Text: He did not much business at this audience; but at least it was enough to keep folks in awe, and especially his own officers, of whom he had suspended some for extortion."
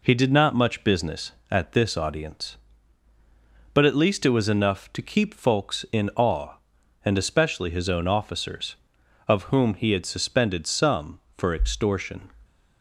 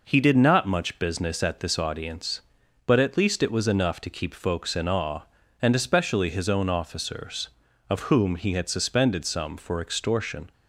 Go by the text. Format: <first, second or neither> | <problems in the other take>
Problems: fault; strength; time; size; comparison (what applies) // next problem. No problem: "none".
neither | none